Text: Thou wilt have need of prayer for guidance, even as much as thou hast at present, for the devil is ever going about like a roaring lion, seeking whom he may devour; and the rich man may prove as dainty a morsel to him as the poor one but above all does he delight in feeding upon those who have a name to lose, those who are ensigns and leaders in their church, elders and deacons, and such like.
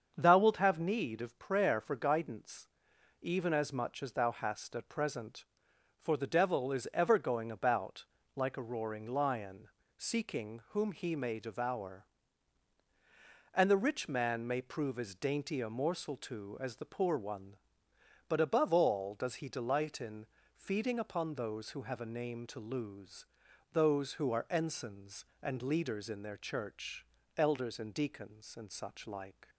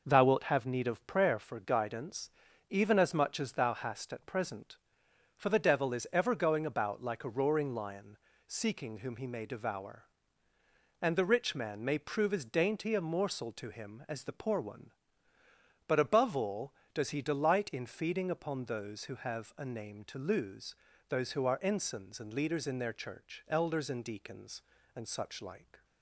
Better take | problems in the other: second | starts louder than the rest; until 1.1 s; 7 dB // pauses between "about" and "like"; slight; at 8.0 s; 0.30 s long // skips "him"; at 16.5 s // pauses between "in" and "feeding"; slight; at 20.2 s; 0.30 s long

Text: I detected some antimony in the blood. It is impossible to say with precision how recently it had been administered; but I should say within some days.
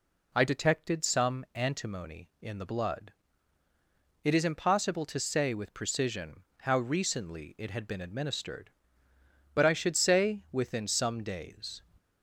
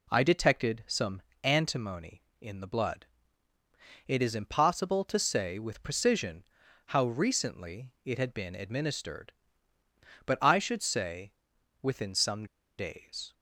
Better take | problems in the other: first | pauses between "some" and "antimony"; slight; at 1.2 s; 0.22 s long // pauses between "precision" and "how"; at 6.4 s; 0.42 s long; slight in the first // pauses between "say" and "within"; noticeable; at 11.3 s; 0.50 s long // pauses between "some" and "days"; slight; at 12.4 s; 0.31 s long

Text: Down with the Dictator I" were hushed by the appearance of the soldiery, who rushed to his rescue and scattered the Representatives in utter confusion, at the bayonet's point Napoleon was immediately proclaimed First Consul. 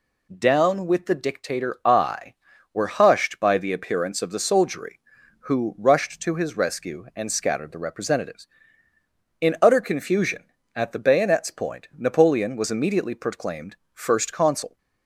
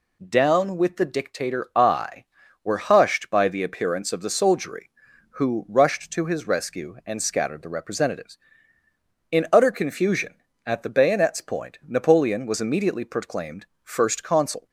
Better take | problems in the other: neither | pauses between "proclaimed" and "First"; slight; the same in both

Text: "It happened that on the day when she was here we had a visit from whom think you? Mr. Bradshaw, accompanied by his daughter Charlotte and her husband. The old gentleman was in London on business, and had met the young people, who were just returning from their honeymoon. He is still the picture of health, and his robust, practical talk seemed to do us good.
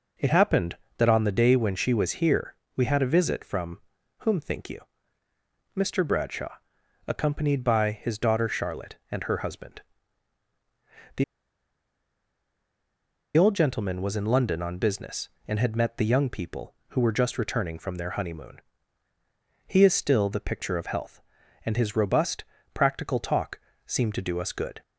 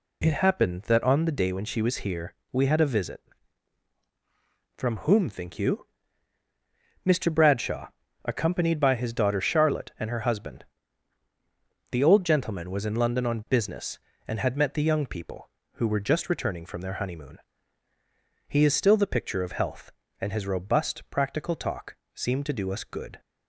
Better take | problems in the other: second | pauses between "here" and "we"; slight; at 2.5 s; 0.22 s long; slight in the second // pauses between "from" and "whom"; at 3.8 s; 0.38 s long // pauses between "The" and "old"; strong; at 11.2 s; 2.1 s long // pauses between "talk" and "seemed"; slight; at 23.5 s; 0.26 s long; slight in the second

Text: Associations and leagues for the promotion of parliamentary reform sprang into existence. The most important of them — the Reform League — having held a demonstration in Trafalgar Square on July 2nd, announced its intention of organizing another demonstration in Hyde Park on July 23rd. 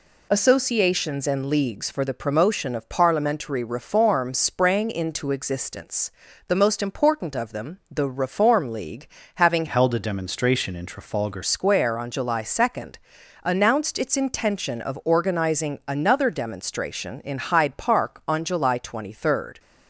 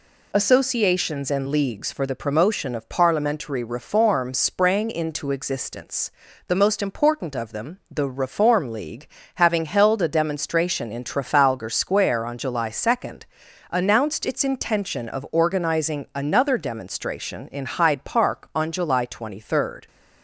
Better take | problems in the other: second | changes voice from "held" to "Trafalgar"; from 9.6 to 11.4 s; 1.8 s long

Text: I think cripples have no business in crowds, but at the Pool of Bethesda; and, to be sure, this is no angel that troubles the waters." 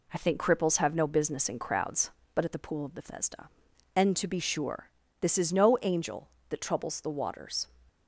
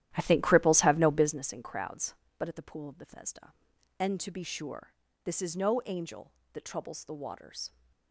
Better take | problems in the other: first | starts louder than the rest; strong; until 1.5 s; 12.5 dB

